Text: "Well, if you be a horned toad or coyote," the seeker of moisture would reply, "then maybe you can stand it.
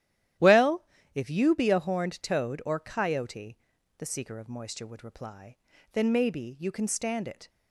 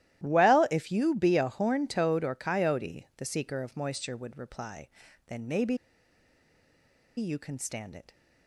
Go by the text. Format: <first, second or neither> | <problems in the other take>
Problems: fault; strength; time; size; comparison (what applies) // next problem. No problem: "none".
first | starts louder than the rest; strong; until 1.2 s; 13.5 dB; strong in the first // pauses between "maybe" and "you"; strong; at 5.7 s; 1.4 s long